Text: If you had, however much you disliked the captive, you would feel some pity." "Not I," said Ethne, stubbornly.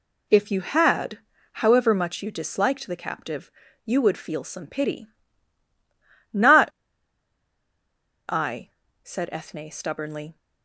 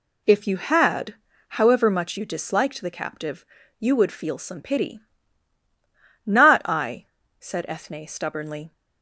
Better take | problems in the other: second | pauses between "Not" and "I"; strong; at 6.6 s; 1.6 s long

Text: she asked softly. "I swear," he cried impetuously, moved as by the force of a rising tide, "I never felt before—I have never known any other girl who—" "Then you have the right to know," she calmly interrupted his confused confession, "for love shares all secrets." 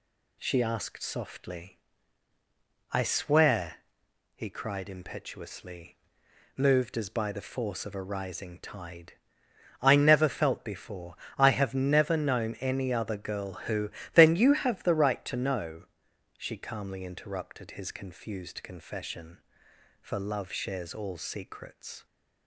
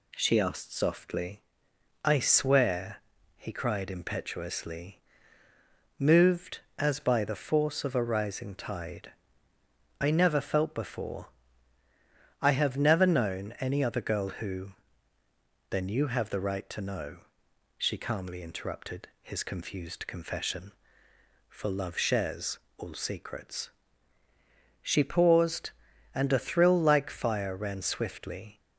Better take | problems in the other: first | pauses between "shares" and "all"; slight; at 22.5 s; 0.18 s long // goes on to say "She paused and a thrill like fire ran swiftly"; strong; from 24.8 s on; 3.7 s long

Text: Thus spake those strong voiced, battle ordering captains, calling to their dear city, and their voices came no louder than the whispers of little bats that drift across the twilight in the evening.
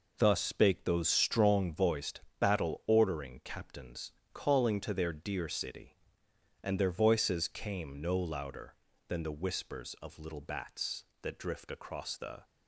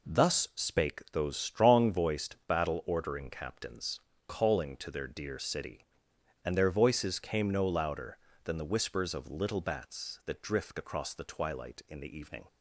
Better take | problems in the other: second | stops before "twilight in the evening"; at 12.4 s

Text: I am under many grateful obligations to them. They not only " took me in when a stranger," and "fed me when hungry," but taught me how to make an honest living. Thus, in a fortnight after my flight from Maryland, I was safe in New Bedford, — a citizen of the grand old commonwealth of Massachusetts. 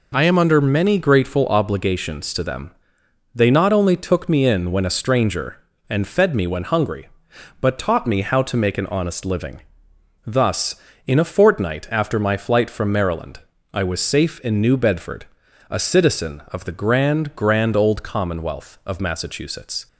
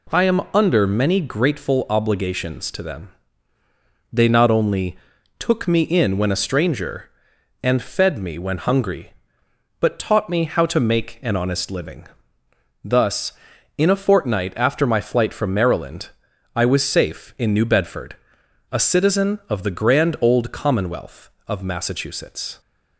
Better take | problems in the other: second | says "grand" twice; at 17.3 s

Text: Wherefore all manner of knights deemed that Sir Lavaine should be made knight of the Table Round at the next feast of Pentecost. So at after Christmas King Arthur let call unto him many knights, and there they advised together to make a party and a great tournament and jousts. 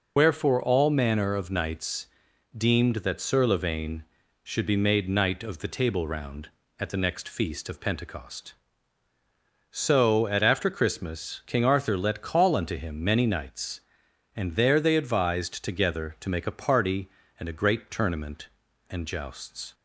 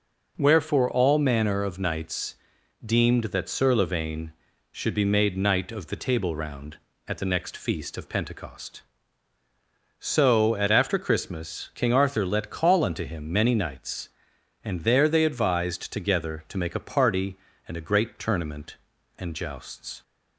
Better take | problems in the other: second | loses the start of "Wherefore"; at 0.1 s; 85 ms // pauses between "knights" and "deemed"; noticeable; at 2.0 s; 0.50 s long; noticeable in the second

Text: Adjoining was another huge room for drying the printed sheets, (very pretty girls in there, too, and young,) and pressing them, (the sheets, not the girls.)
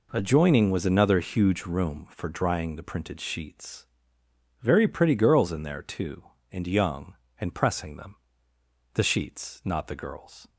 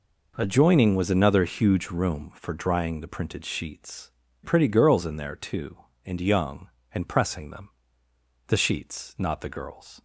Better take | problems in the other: first | skips "very"; at 4.2 s

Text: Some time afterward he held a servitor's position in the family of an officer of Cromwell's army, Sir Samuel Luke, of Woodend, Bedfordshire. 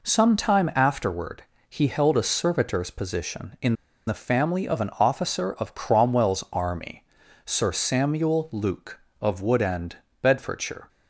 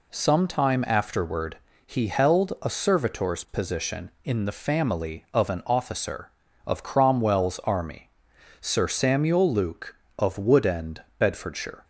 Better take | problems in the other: second | pauses between "afterward" and "he"; slight; at 1.4 s; 0.26 s long; slight in the second // pauses between "in" and "the"; slight; at 3.7 s; 0.32 s long

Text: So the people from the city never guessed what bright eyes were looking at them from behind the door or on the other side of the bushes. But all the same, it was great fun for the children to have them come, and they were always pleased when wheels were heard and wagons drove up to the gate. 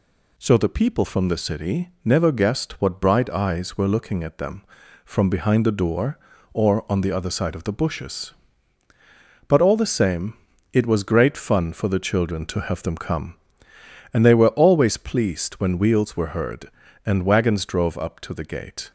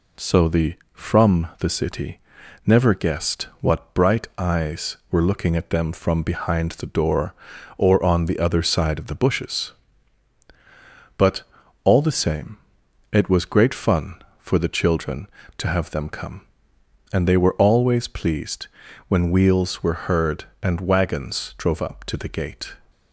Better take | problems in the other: first | skips "people"; at 0.8 s // pauses between "city" and "never"; noticeable; at 2.1 s; 0.46 s long; slight in the first // pauses between "But" and "all"; at 11.4 s; 0.42 s long // pauses between "pleased" and "when"; at 18.6 s; 0.40 s long

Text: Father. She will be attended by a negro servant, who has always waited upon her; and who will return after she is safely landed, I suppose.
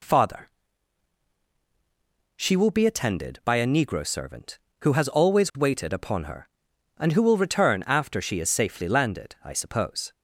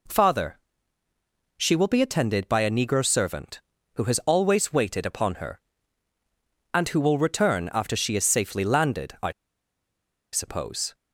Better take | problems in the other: first | pauses between "I" and "suppose"; at 9.3 s; 1.0 s long

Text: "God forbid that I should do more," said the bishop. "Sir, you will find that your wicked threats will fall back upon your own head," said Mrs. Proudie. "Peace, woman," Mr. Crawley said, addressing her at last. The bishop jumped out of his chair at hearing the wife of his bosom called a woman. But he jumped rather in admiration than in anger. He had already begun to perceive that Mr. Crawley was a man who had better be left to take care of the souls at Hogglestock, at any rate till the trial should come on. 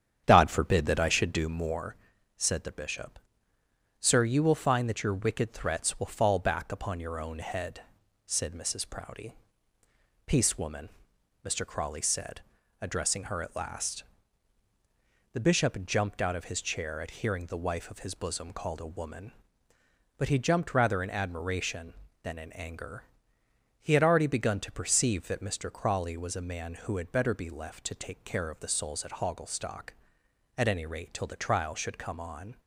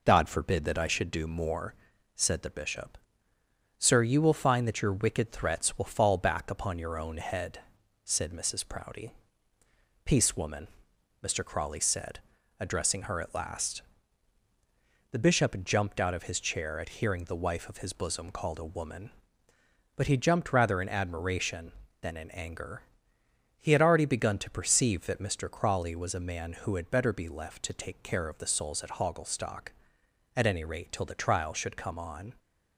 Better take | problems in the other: second | starts louder than the rest; strong; until 1.7 s; 8.5 dB

